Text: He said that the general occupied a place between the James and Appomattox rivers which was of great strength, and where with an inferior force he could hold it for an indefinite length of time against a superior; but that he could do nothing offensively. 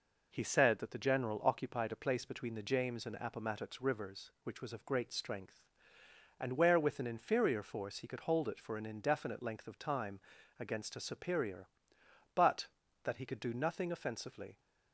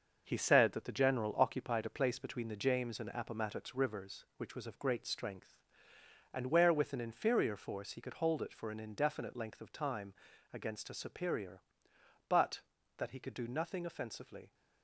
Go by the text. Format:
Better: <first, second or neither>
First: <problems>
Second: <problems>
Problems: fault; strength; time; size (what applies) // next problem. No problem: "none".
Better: first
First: pauses between "time" and "against"; slight; at 10.2 s; 0.36 s long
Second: gets quieter; throughout; 7 dB // pauses between "time" and "against"; slight; at 10.1 s; 0.36 s long